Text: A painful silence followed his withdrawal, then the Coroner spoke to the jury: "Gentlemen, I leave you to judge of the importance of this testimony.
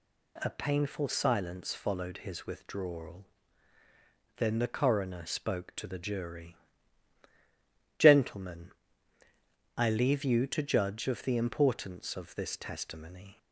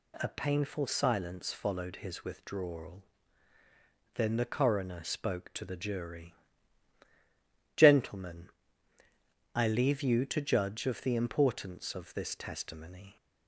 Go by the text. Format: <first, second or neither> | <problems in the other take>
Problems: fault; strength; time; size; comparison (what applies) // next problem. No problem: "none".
neither | none